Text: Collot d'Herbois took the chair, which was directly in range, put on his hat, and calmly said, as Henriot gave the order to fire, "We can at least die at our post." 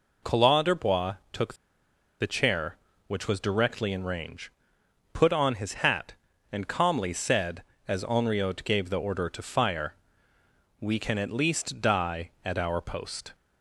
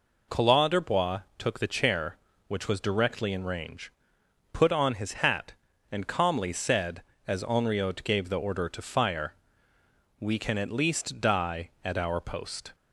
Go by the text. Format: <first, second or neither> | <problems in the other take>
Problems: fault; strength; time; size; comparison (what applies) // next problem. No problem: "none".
second | pauses between "d'Herbois" and "took"; slight; at 1.1 s; 0.16 s long; slight in the second // pauses between "took" and "the"; noticeable; at 1.5 s; 0.65 s long